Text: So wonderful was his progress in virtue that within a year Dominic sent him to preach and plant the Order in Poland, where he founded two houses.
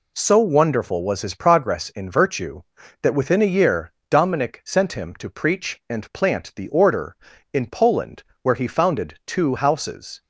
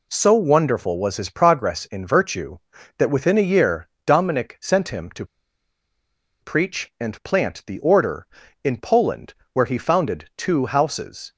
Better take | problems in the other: first | pauses between "year" and "Dominic"; slight; at 3.8 s; 0.20 s long; slight in the first // pauses between "to" and "preach"; at 5.2 s; 1.1 s long

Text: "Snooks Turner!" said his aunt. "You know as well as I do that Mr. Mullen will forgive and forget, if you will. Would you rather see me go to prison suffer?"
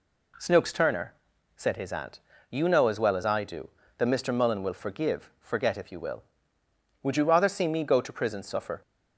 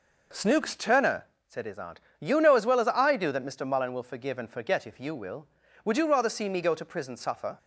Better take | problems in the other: second | skips "and"; at 5.3 s

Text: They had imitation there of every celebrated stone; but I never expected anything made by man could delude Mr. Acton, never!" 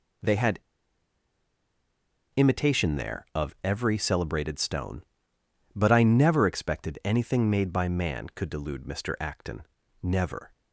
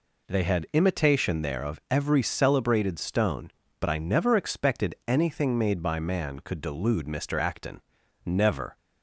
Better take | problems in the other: second | pauses between "had" and "imitation"; strong; at 0.5 s; 1.7 s long

